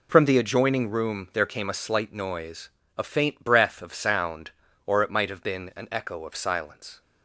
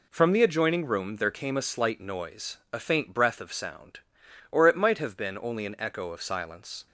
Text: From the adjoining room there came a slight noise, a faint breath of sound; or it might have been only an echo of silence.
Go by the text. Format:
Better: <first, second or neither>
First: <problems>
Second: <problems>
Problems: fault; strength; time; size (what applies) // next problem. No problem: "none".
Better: second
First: skips "only"; at 5.7 s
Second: none